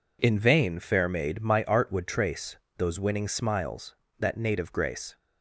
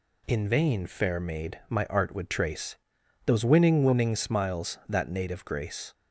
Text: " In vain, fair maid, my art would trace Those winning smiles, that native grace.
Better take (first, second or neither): first